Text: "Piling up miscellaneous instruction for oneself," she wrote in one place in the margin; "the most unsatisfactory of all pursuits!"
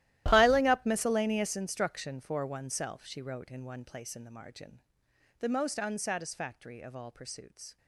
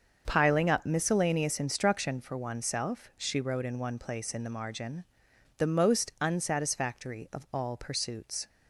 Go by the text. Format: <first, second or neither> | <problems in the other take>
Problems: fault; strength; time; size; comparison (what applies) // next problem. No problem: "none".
second | gets quieter; strong; throughout; 18 dB // starts louder than the rest; strong; until 1.2 s; 14.5 dB; also in the second